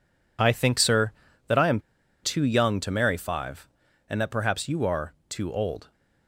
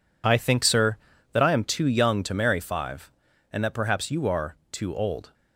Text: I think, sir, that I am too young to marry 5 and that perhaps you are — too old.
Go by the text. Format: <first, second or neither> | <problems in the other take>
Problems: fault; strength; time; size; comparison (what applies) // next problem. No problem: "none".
second | pauses between "am" and "too"; at 1.7 s; 0.43 s long